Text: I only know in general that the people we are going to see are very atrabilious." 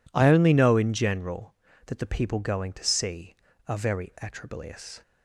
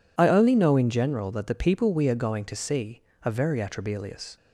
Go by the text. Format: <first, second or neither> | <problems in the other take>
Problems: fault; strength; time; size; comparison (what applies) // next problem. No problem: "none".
second | skips "we are"; at 2.3 s